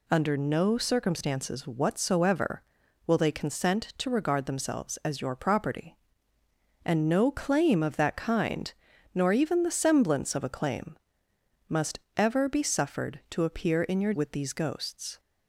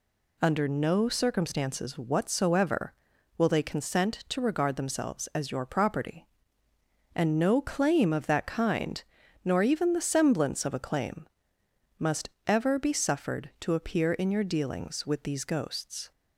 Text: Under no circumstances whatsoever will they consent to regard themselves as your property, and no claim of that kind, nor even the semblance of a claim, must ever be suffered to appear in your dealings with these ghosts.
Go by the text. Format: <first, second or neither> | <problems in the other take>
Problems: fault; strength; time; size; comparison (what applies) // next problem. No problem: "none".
second | pauses between "must" and "ever"; slight; at 11.9 s; 0.18 s long; slight in the second // skips "dealings"; at 14.1 s